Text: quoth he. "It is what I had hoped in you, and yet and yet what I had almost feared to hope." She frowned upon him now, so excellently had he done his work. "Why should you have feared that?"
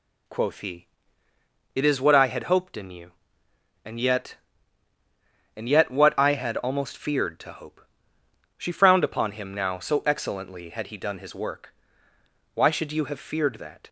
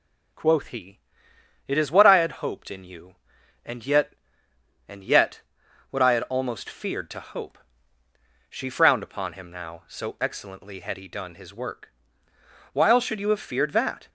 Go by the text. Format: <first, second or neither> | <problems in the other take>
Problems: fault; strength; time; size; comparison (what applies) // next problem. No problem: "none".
first | pauses between "yet" and "what"; noticeable; at 5.4 s; 0.50 s long // says "While" for "Why"; at 12.7 s